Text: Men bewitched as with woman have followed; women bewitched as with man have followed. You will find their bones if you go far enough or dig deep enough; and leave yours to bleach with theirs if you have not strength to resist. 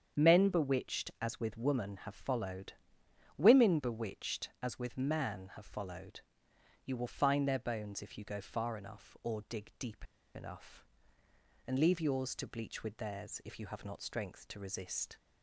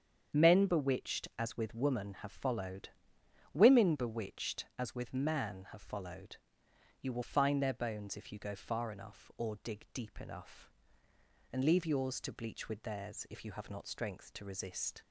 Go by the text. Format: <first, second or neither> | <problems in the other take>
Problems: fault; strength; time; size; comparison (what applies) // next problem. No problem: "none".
second | starts louder than the rest; strong; until 1.2 s; 8 dB; strong in the second // pauses between "deep" and "enough"; slight; at 10.0 s; 0.30 s long